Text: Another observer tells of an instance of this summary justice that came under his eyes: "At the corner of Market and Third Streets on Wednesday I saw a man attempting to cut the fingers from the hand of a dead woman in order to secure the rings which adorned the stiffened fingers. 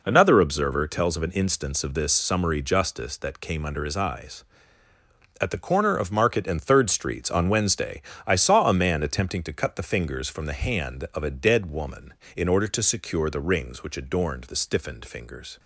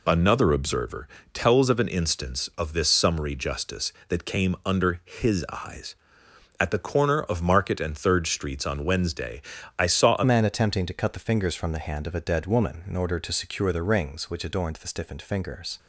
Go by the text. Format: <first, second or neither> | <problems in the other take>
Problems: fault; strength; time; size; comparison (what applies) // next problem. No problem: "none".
first | pauses between "observer" and "tells"; slight; at 1.0 s; 0.28 s long // pauses between "Wednesday" and "I"; slight; at 9.4 s; 0.36 s long; slight in the first // changes voice at "man"; from 10.2 s on; 5.5 s long